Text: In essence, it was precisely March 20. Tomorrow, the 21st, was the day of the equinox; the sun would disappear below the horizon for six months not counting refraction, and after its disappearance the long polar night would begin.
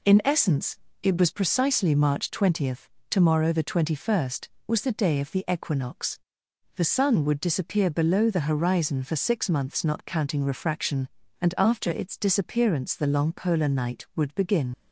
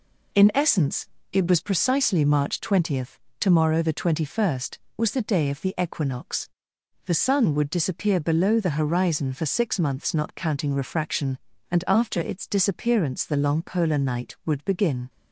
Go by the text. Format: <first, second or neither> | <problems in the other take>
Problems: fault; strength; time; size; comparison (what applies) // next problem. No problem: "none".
second | leaves "begin" unfinished; at 14.7 s; 55 ms